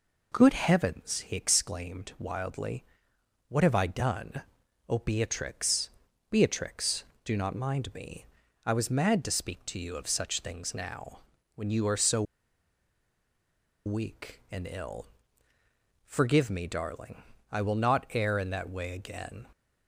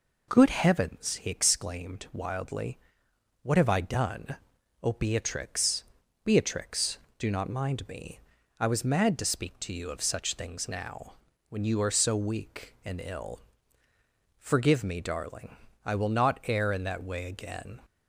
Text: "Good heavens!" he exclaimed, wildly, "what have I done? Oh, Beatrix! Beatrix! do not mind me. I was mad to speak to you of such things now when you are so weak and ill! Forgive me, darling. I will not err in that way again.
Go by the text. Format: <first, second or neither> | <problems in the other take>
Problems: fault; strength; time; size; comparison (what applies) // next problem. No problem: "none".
second | pauses between "now" and "when"; slight; at 11.1 s; 0.36 s long; slight in the second // pauses between "so" and "weak"; strong; at 12.2 s; 1.6 s long